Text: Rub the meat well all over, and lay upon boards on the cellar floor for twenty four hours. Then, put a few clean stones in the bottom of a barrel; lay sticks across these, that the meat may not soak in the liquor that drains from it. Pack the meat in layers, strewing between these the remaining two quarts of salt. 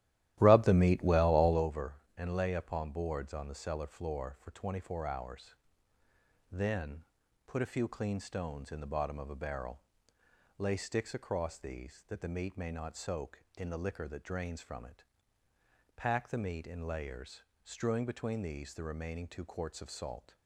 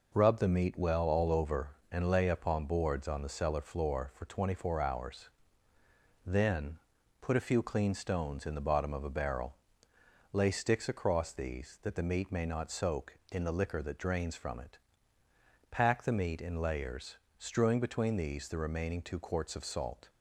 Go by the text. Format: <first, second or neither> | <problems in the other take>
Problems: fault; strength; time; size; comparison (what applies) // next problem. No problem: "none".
second | starts louder than the rest; strong; until 1.7 s; 14 dB